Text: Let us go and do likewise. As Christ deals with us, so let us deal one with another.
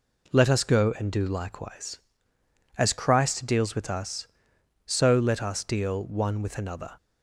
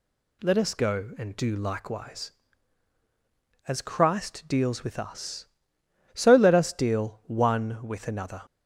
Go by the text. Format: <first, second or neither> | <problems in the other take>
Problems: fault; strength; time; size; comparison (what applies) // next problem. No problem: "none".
neither | none